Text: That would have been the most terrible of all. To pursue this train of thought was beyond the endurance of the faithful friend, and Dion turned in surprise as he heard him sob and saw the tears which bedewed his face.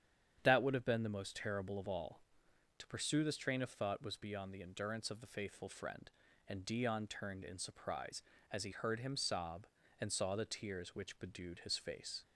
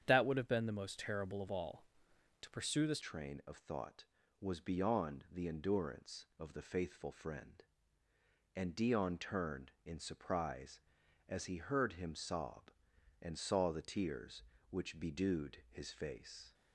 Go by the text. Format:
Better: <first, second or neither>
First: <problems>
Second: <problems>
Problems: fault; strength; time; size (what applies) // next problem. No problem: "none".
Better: first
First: starts louder than the rest; strong; until 1.4 s; 9 dB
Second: starts louder than the rest; strong; until 1.0 s; 8.5 dB // changes voice at "train"; from 3.0 s on; 13.5 s long